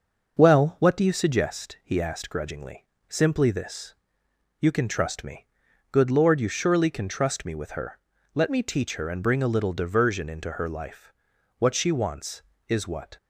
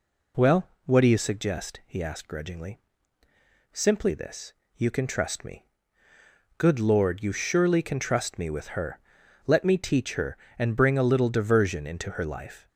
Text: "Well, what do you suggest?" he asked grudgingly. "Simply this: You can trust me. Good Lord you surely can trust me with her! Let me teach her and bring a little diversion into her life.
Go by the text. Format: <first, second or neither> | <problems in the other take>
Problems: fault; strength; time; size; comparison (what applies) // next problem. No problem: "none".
second | starts louder than the rest; noticeable; until 1.4 s; 6 dB // goes on to say "What she wants is what"; from 11.5 s on; 1.6 s long